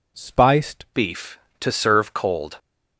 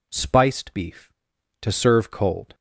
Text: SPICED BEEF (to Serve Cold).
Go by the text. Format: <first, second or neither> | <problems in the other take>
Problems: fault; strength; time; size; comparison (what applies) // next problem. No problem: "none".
second | changes voice at "BEEF"; from 0.9 s on; 1.6 s long